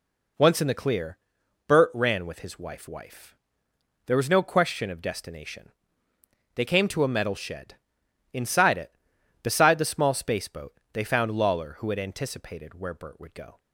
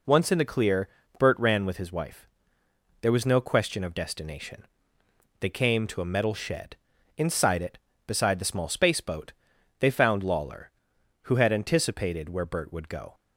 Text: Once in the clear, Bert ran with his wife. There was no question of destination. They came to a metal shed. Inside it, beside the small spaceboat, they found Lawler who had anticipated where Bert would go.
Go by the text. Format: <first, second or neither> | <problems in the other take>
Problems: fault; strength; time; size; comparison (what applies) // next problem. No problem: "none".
second | says "wife" twice; at 2.8 s